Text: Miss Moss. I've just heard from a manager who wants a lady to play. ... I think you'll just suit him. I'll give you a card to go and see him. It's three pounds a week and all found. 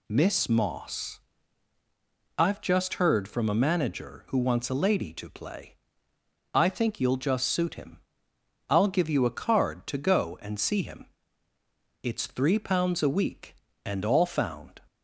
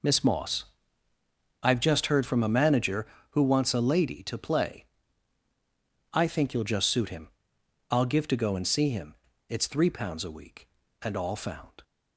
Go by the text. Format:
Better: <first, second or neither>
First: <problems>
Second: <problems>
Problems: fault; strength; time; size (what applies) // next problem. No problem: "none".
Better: first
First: none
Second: skips "you a card"; at 8.2 s